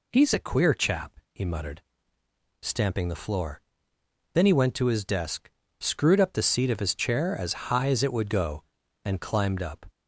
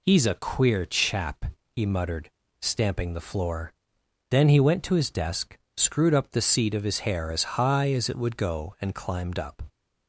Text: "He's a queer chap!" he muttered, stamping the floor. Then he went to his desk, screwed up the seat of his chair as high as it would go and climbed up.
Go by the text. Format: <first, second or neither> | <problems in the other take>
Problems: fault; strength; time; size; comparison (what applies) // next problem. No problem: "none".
first | says "hair" for "chair"; at 6.9 s